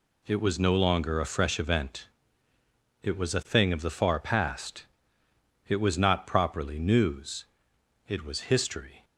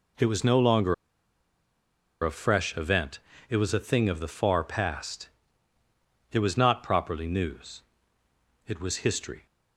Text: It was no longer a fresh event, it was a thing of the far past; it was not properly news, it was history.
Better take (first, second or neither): first